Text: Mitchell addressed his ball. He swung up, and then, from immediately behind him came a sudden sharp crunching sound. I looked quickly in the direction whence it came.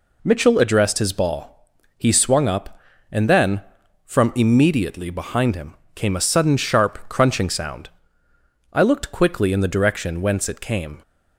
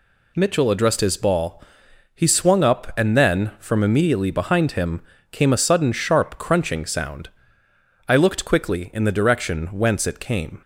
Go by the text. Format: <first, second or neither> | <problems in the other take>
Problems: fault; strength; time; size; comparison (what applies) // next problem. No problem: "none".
neither | pauses between "him" and "came"; slight; the same in both